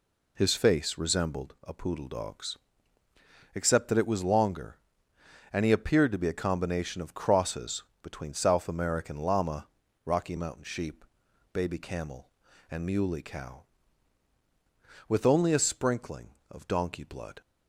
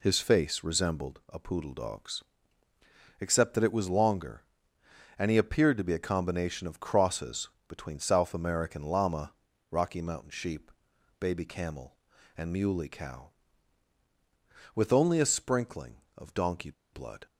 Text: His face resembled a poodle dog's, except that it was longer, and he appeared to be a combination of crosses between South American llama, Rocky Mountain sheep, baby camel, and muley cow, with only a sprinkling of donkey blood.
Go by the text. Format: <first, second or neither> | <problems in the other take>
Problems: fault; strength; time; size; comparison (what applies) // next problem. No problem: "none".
first | pauses between "crosses" and "between"; slight; at 7.4 s; 0.18 s long; slight in the first // pauses between "donkey" and "blood"; slight; at 16.7 s; 0.21 s long